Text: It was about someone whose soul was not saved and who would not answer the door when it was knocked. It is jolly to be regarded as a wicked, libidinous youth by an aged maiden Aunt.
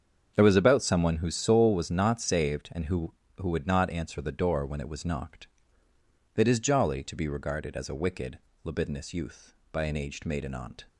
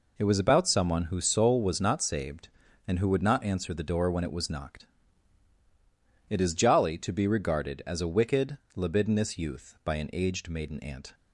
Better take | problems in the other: second | starts louder than the rest; strong; until 1.3 s; 7 dB // says "who" twice; at 3.3 s

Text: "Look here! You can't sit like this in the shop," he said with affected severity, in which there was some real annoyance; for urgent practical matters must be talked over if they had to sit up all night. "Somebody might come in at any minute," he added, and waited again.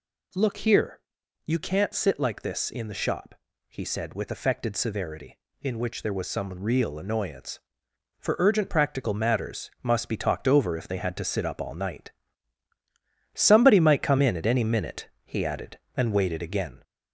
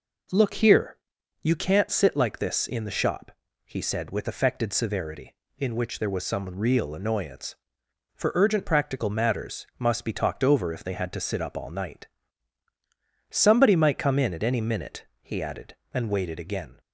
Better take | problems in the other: second | gets louder; slight; throughout; 2.5 dB

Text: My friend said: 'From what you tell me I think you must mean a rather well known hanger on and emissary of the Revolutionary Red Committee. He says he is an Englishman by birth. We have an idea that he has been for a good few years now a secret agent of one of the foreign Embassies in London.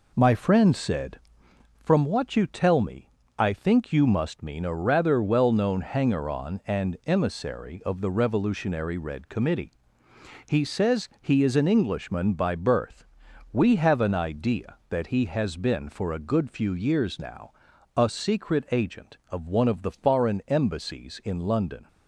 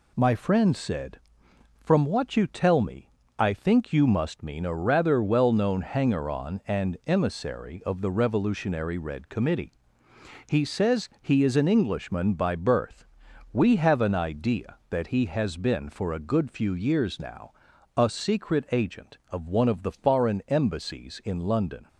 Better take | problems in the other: second | starts louder than the rest; until 1.6 s; 4 dB // pauses between "me" and "I"; slight; at 3.0 s; 0.30 s long; slight in the second // pauses between "now" and "a"; noticeable; at 17.5 s; 0.46 s long; noticeable in the second

